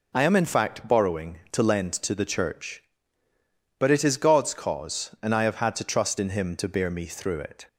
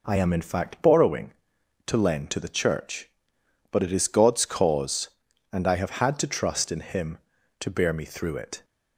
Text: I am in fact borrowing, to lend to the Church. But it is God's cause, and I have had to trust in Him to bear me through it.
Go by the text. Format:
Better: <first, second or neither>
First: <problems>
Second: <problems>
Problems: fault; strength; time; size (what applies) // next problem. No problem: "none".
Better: neither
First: none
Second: none